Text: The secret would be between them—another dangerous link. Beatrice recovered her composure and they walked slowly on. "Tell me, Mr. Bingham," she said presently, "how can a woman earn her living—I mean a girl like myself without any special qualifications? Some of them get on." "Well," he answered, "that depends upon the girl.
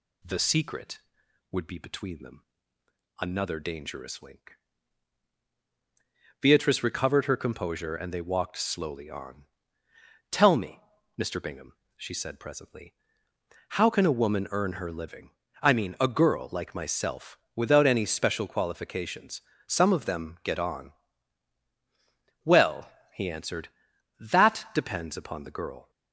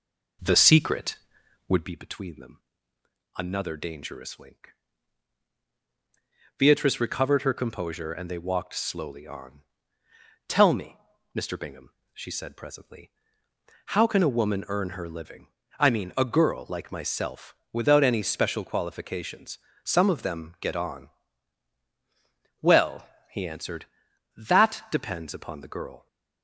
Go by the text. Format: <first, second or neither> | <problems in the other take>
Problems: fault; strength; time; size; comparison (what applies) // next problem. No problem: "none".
first | starts louder than the rest; noticeable; until 2.0 s; 4.5 dB // pauses between "myself" and "without"; slight; at 17.5 s; 0.20 s long; slight in the first